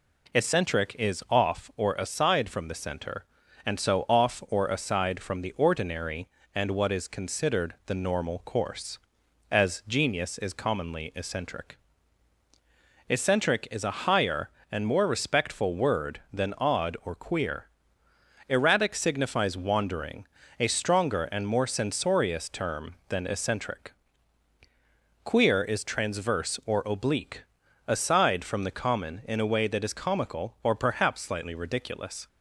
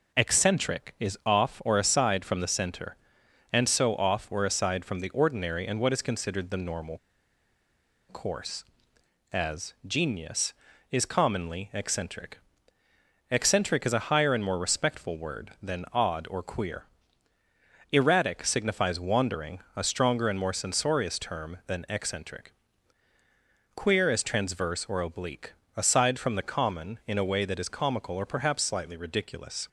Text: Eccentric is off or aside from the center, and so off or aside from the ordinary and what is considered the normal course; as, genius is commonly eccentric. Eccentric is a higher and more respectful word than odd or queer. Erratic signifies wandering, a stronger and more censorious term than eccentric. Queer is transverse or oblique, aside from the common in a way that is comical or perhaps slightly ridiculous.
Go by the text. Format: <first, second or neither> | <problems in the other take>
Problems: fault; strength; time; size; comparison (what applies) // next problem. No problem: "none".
first | pauses between "normal" and "course"; at 6.9 s; 1.0 s long